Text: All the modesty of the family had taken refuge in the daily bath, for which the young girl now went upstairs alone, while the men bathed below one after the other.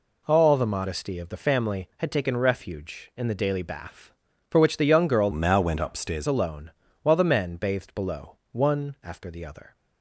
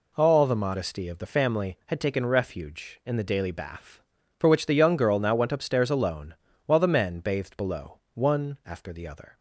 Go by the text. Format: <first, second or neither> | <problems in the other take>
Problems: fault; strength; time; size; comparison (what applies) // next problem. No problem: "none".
second | changes voice from "now" to "upstairs"; from 5.3 to 6.2 s; 0.9 s long